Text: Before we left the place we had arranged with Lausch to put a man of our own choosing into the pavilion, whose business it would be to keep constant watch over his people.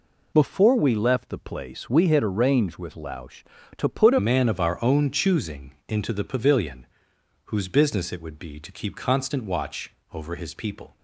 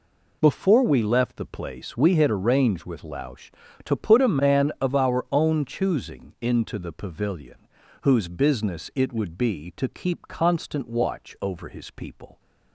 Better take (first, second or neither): second